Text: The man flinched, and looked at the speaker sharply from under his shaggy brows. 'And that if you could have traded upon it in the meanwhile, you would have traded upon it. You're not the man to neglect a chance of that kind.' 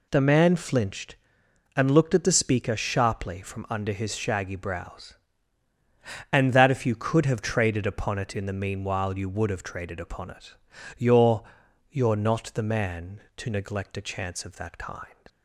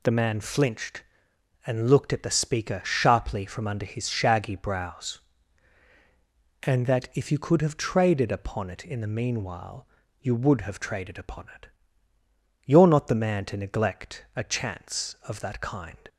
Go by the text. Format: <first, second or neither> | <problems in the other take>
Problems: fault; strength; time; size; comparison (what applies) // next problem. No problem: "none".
second | says "You're" twice; at 11.9 s